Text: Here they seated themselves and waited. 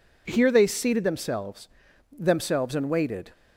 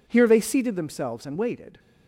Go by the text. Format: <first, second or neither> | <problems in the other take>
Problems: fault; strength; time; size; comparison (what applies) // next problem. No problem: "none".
second | says "themselves" twice; at 2.1 s